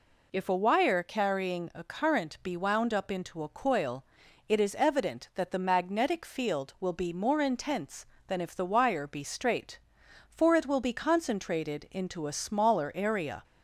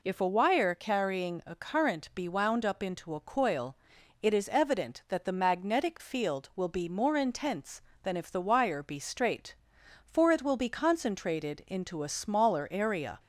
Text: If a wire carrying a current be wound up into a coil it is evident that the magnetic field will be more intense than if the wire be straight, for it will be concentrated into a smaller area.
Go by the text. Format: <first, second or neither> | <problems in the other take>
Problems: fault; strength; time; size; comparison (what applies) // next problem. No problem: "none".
neither | pauses between "coil" and "it"; the same in both